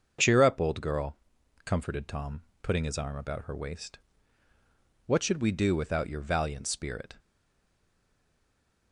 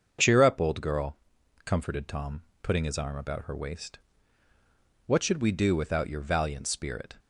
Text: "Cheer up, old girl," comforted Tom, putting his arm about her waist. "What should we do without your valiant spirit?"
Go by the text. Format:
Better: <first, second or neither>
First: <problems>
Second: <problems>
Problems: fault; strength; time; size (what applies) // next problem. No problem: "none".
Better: second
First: starts louder than the rest; until 1.6 s; 6.5 dB // stays silent after the last word; noticeable; from 7.1 s on; 1.8 s long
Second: starts louder than the rest; until 1.6 s; 6.5 dB